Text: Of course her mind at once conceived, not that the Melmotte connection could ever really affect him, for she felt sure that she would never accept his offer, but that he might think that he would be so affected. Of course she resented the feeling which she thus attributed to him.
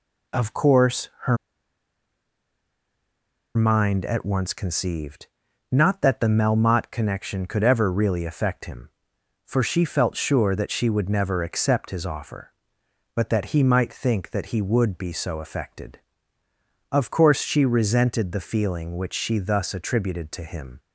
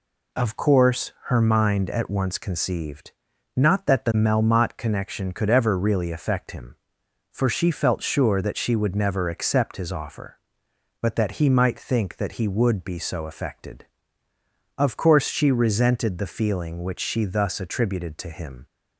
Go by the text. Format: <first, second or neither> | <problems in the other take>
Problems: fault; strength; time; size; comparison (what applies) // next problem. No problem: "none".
second | pauses between "her" and "mind"; strong; at 1.3 s; 2.2 s long